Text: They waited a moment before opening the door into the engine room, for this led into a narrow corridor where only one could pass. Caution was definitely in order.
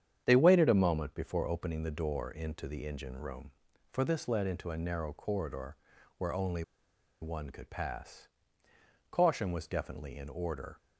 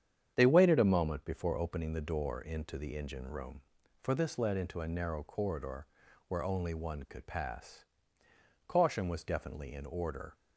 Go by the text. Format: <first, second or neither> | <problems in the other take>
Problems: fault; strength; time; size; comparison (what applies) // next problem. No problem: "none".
second | starts louder than the rest; strong; until 1.2 s; 8.5 dB; strong in the second // pauses between "corridor" and "where"; at 5.7 s; 0.42 s long; also in the second // pauses between "only" and "one"; noticeable; at 6.6 s; 0.58 s long